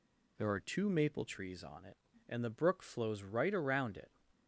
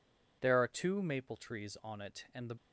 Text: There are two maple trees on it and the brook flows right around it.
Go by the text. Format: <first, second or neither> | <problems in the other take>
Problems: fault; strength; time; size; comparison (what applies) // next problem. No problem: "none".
first | stops before "brook flows right around it"; at 2.5 s